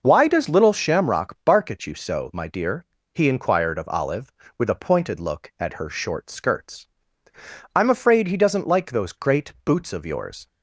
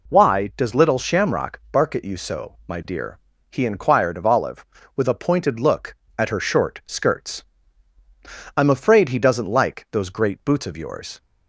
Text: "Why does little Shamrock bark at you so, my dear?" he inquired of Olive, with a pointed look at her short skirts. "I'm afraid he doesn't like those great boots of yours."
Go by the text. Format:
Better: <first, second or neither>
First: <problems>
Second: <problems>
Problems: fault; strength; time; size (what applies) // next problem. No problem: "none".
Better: neither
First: none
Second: none